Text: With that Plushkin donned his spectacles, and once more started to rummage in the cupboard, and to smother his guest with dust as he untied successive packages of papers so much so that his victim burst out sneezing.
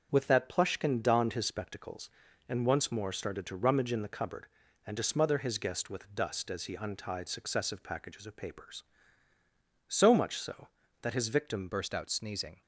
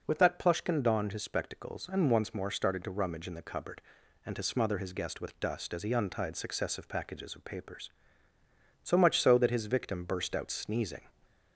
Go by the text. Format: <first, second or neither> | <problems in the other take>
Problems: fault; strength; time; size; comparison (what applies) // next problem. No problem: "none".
second | starts louder than the rest; until 1.1 s; 7 dB // changes voice at "burst"; from 11.6 s on; 1.0 s long